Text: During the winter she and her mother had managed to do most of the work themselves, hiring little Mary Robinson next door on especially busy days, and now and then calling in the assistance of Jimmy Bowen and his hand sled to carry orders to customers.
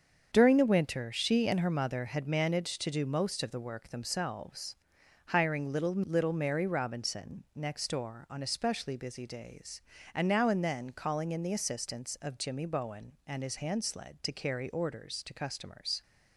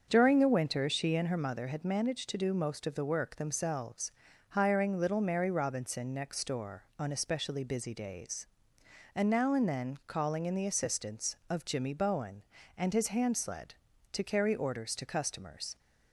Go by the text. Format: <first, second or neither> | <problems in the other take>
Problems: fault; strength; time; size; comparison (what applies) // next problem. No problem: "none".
second | starts louder than the rest; until 1.3 s; 7 dB; also in the second // says "little" twice; at 5.9 s